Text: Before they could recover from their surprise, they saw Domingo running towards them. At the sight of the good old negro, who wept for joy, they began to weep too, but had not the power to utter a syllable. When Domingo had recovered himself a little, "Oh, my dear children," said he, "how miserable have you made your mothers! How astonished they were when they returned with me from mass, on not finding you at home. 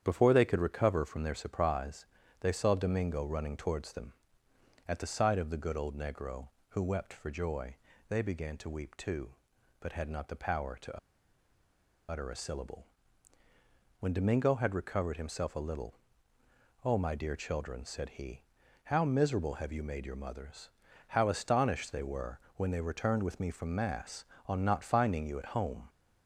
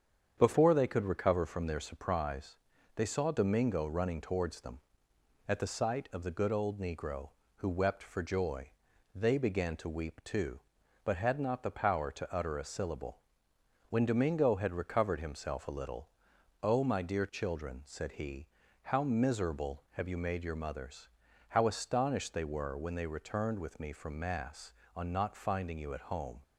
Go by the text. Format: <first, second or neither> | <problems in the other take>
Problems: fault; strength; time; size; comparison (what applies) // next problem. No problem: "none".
second | starts louder than the rest; strong; until 1.0 s; 9 dB; strong in the second // pauses between "to" and "utter"; at 10.9 s; 1.1 s long // pauses between "were" and "when"; slight; at 22.3 s; 0.18 s long